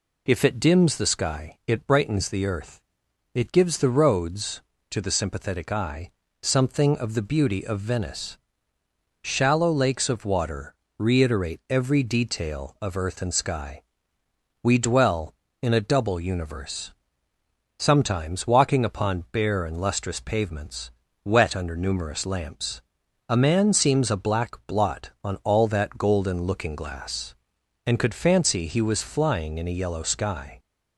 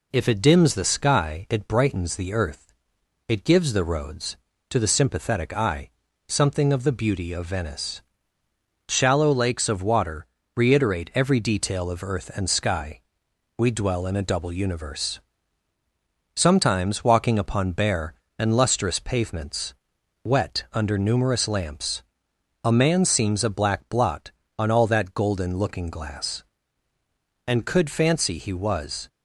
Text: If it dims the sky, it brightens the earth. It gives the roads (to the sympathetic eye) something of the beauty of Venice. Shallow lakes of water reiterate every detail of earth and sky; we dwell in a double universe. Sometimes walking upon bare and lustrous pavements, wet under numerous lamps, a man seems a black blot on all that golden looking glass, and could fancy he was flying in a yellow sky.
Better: first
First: pauses between "water" and "reiterate"; slight; at 10.7 s; 0.24 s long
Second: pauses between "water" and "reiterate"; slight; at 10.2 s; 0.28 s long // stops before "flying in a yellow sky"; at 29.0 s

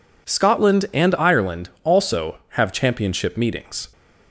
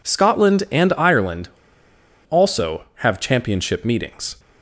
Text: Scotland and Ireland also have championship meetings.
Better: first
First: none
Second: pauses between "Ireland" and "also"; noticeable; at 1.4 s; 0.80 s long

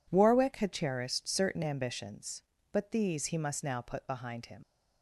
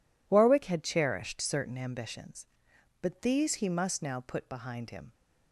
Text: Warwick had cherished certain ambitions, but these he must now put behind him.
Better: second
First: leaves "him" unfinished; at 4.6 s; 75 ms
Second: none

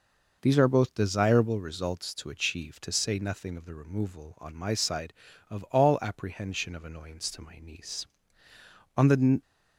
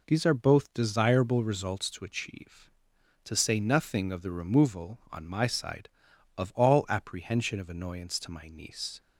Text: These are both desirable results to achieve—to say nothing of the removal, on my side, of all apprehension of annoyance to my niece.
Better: second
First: goes on to say "On the"; slight; from 8.9 s on; 0.44 s long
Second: none

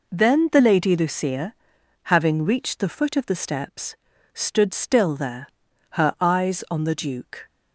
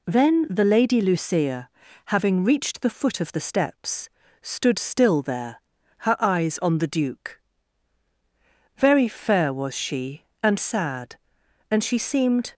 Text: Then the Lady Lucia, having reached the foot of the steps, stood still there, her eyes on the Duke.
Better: first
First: none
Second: goes on to say "Very fair was she and sad and she seemed"; strong; from 8.7 s on; 3.7 s long

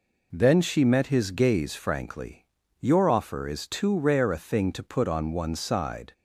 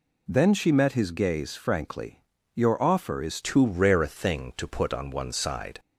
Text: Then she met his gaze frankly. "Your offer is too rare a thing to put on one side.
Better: first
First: none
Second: changes voice at "too"; from 3.4 s on; 2.3 s long

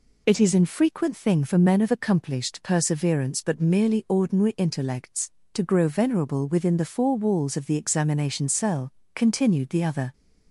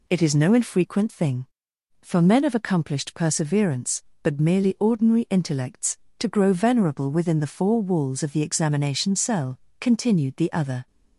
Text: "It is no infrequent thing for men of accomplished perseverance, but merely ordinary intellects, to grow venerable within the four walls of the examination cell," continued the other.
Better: second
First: skips "no"; at 0.5 s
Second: none

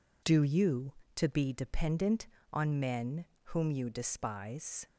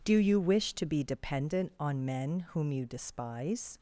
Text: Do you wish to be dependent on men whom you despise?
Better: second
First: skips "wish"; at 1.0 s // pauses between "men" and "whom"; slight; at 3.2 s; 0.18 s long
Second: none

